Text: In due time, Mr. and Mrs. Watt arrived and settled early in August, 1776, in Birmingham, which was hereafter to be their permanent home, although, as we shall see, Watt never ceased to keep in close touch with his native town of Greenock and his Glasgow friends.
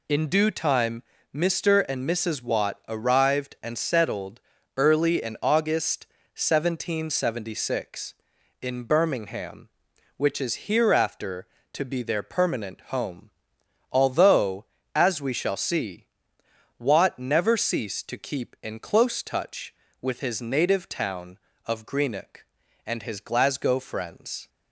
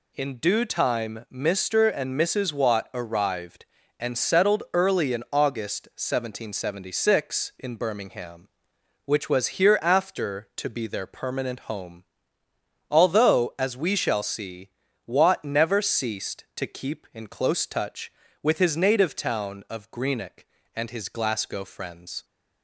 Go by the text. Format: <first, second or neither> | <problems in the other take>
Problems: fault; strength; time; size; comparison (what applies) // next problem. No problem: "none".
second | pauses between "settled" and "early"; slight; at 4.4 s; 0.36 s long // says "is" for "was"; at 10.4 s